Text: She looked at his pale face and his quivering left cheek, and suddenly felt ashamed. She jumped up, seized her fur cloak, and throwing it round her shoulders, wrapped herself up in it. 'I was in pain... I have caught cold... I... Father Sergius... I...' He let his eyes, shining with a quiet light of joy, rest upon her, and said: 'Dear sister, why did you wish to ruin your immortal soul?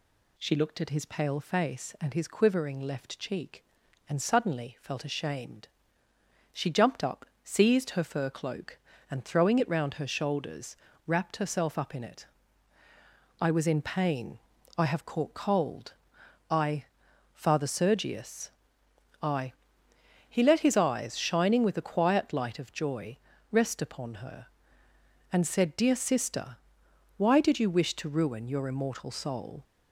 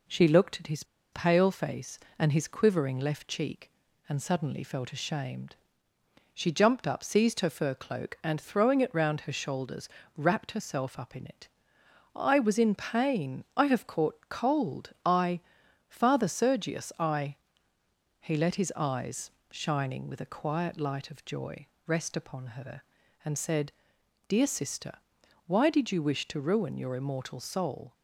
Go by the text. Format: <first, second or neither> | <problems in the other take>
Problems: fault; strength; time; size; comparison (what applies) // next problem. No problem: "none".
first | pauses between "his" and "pale"; slight; at 0.8 s; 0.29 s long